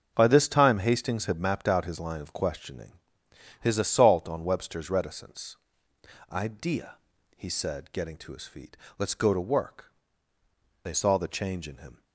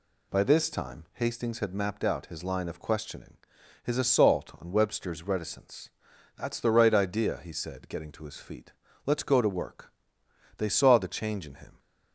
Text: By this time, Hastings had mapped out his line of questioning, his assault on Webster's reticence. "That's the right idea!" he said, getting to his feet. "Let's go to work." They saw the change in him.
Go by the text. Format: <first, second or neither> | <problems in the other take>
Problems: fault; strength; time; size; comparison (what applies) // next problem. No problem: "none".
second | starts louder than the rest; until 1.1 s; 7 dB // skips "That's the right"; at 5.9 s